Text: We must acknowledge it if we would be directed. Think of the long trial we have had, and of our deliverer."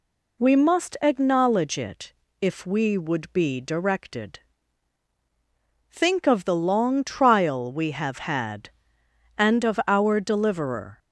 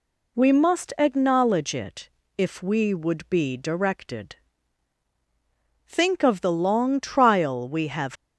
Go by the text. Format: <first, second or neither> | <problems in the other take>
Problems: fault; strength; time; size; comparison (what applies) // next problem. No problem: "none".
first | pauses between "it" and "if"; slight; at 2.0 s; 0.28 s long; slight in the first // stops before "had and of our deliverer"; at 8.1 s